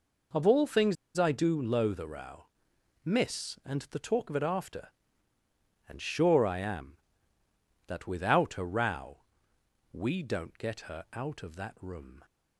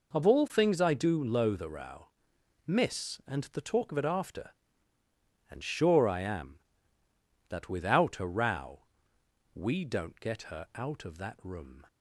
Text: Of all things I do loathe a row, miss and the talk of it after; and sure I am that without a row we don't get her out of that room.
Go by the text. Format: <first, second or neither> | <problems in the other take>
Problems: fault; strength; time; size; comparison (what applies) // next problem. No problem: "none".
second | pauses between "things" and "I"; slight; at 0.9 s; 0.21 s long // pauses between "row" and "we"; noticeable; at 9.2 s; 0.72 s long; noticeable in the second